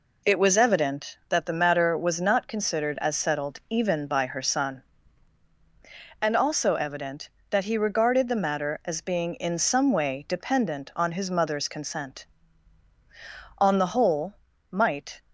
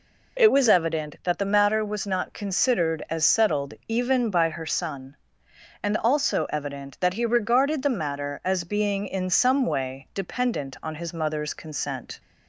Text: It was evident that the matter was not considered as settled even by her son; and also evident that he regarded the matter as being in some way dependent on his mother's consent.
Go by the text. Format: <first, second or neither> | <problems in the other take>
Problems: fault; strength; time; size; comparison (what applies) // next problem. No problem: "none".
second | goes on to say "On the whole might"; from 13.5 s on; 1.6 s long